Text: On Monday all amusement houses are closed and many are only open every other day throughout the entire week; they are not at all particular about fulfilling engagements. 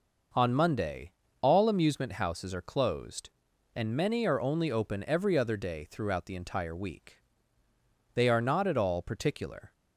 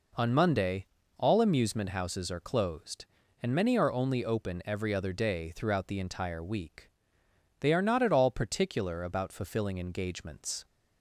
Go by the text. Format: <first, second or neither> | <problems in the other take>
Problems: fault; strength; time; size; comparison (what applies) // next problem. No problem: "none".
second | pauses between "Monday" and "all"; slight; at 1.1 s; 0.32 s long; slight in the second // stops before "about fulfilling engagements"; at 9.7 s